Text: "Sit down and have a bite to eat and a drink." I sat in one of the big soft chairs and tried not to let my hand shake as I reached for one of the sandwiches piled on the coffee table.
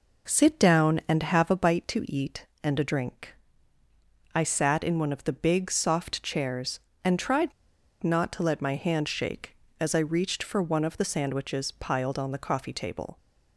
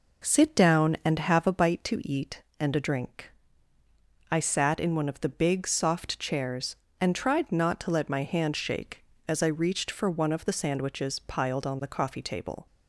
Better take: second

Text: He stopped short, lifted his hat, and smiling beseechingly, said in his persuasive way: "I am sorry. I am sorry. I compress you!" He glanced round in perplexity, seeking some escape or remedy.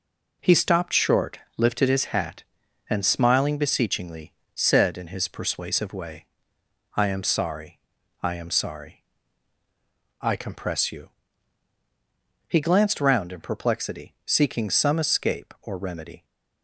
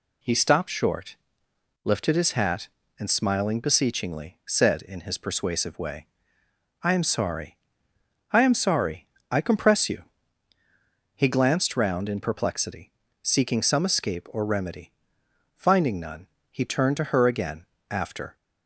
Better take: first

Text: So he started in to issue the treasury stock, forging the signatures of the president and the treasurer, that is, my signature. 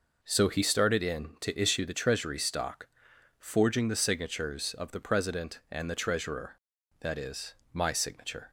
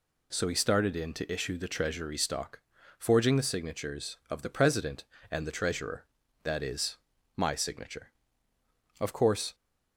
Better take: first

